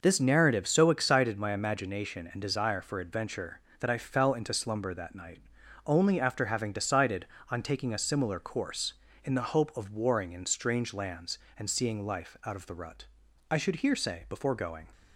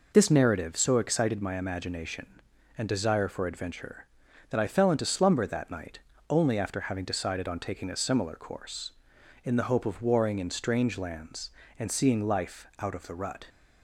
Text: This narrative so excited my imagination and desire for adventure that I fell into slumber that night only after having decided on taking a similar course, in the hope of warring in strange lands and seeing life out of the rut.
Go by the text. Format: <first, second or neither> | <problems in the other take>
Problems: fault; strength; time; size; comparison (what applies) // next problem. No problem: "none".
second | pauses between "night" and "only"; noticeable; at 5.3 s; 0.48 s long; slight in the second // goes on to say "I should here say before going"; from 13.4 s on; 1.4 s long